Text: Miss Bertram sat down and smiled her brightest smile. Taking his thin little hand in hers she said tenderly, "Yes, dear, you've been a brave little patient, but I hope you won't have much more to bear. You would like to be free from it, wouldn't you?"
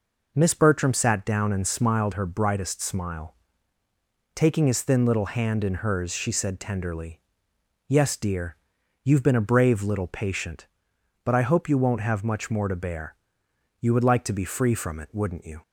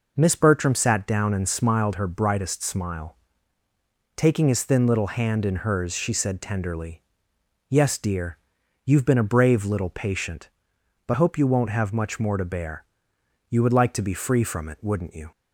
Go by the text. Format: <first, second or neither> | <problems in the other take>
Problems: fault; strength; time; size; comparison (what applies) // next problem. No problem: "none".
first | skips "I"; at 11.1 s